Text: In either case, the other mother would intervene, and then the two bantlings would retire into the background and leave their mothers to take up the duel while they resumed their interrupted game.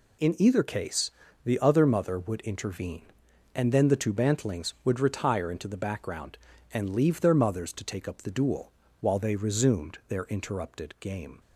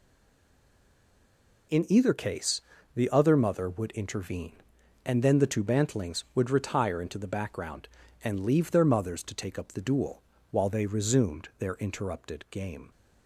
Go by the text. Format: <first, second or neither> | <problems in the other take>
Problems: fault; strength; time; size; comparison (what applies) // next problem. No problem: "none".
first | stays silent before the first word; noticeable; until 1.7 s; 1.7 s long // pauses between "duel" and "while"; slight; at 10.2 s; 0.30 s long; slight in the first